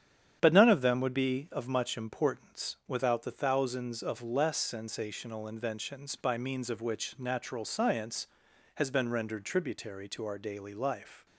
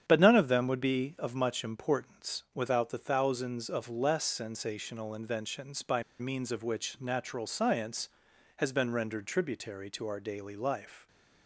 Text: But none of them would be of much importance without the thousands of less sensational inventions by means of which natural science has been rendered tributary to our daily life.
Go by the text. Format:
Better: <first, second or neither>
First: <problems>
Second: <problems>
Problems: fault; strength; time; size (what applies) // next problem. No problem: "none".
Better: first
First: starts louder than the rest; strong; until 1.4 s; 9 dB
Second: starts louder than the rest; strong; until 1.0 s; 9 dB // pauses between "by" and "means"; slight; at 6.0 s; 0.16 s long